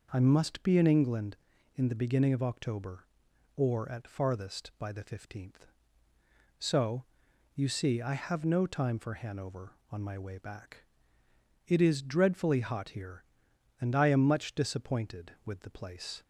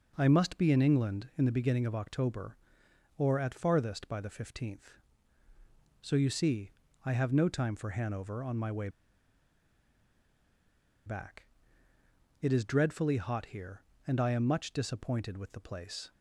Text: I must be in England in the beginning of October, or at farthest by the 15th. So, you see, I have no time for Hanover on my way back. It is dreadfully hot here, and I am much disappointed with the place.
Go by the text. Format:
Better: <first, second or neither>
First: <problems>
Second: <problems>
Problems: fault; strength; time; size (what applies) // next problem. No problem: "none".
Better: first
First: none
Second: pauses between "way" and "back"; strong; at 8.8 s; 2.1 s long